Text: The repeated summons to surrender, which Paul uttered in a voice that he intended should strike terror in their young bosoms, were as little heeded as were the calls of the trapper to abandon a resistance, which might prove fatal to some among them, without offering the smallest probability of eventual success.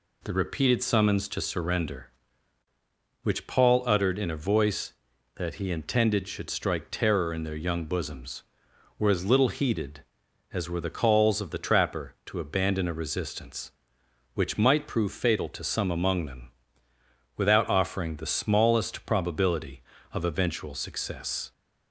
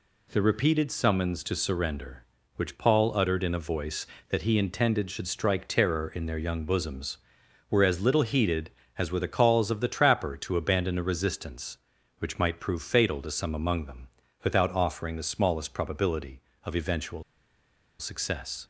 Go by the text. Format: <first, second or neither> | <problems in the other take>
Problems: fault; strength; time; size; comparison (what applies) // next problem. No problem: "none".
first | pauses between "eventual" and "success"; noticeable; at 17.2 s; 0.76 s long